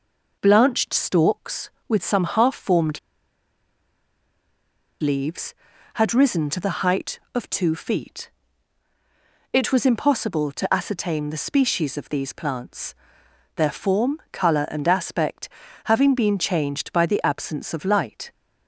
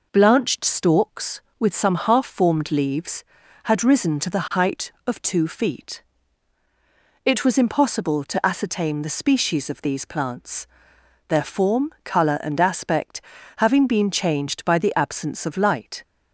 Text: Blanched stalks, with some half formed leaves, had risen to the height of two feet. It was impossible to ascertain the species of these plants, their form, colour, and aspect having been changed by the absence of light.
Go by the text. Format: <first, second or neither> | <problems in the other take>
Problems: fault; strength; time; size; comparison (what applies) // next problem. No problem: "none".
second | pauses between "formed" and "leaves"; strong; at 2.9 s; 2.0 s long // pauses between "aspect" and "having"; slight; at 15.4 s; 0.36 s long; slight in the second